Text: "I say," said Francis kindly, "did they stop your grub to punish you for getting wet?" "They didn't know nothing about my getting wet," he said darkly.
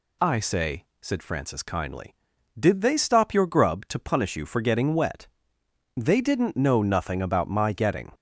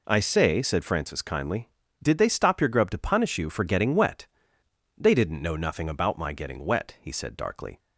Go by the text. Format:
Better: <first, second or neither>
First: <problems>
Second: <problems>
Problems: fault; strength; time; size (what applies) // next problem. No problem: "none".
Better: second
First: stops before "wet he said darkly"; at 8.1 s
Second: none